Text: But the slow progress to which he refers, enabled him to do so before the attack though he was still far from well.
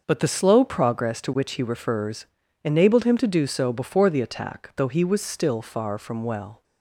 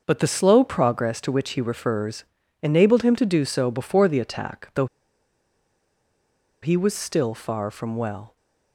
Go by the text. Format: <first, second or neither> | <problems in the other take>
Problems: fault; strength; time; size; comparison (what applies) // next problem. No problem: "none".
first | starts louder than the rest; until 1.0 s; 6 dB; also in the first // pauses between "though" and "he"; strong; at 4.8 s; 1.7 s long